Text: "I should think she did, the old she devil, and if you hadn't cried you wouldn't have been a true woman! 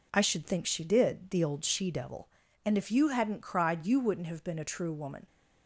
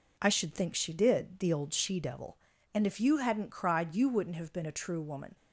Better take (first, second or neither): neither